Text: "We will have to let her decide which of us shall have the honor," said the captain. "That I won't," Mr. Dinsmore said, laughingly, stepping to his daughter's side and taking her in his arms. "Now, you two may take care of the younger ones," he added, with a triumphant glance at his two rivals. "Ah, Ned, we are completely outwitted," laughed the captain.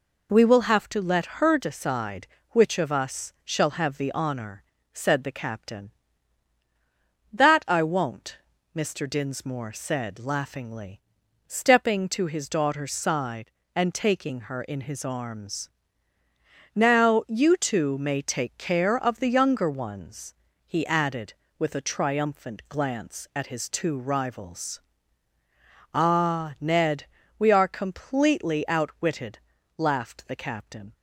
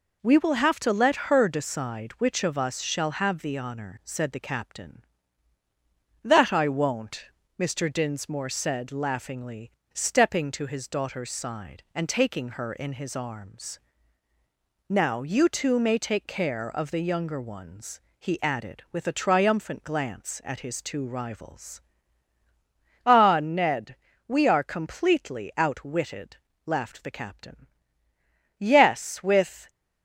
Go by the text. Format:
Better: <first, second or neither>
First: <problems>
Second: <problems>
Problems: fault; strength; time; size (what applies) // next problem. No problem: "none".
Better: first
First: none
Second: goes on to say "Yes with"; noticeable; from 28.5 s on; 1.1 s long